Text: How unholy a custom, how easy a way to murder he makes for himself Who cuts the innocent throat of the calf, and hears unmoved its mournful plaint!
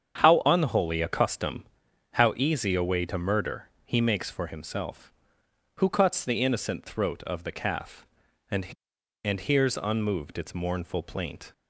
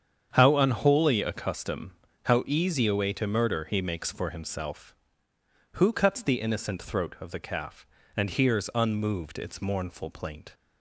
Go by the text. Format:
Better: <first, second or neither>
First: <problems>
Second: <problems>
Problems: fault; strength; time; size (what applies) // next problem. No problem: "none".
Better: second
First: starts louder than the rest; strong; until 1.2 s; 8 dB // pauses between "murder" and "he"; slight; at 3.6 s; 0.16 s long // says "and" twice; at 9.2 s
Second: starts louder than the rest; strong; until 1.3 s; 8 dB